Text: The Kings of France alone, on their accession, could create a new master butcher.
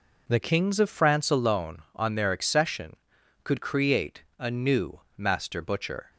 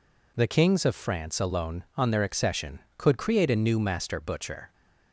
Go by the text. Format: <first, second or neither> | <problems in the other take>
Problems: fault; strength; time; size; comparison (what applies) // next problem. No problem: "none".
second | changes voice at "Kings"; from 0.4 s on; 5.7 s long // pauses between "new" and "master"; slight; at 5.0 s; 0.16 s long